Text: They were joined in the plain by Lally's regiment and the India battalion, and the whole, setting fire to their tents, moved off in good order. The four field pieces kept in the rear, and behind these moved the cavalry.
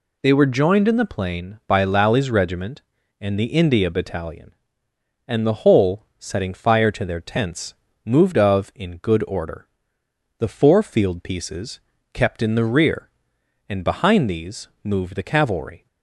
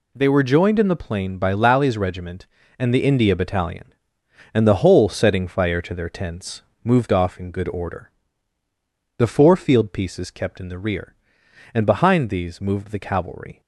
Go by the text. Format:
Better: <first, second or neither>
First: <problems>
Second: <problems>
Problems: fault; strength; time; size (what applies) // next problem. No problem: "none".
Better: second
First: says "of" for "off"; at 8.3 s // pauses between "pieces" and "kept"; slight; at 11.7 s; 0.34 s long // pauses between "these" and "moved"; slight; at 14.6 s; 0.16 s long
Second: none